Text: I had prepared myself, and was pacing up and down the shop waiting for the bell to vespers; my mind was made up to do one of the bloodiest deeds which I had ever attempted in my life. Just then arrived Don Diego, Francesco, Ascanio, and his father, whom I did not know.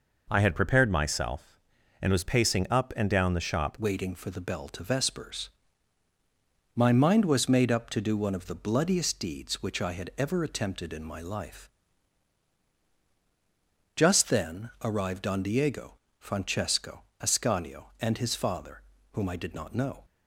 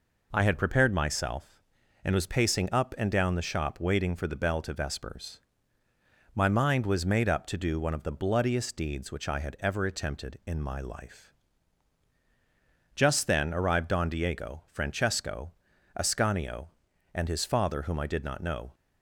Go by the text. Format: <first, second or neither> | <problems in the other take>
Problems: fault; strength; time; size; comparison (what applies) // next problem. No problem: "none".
second | changes voice at "waiting"; from 3.7 s on; 16.3 s long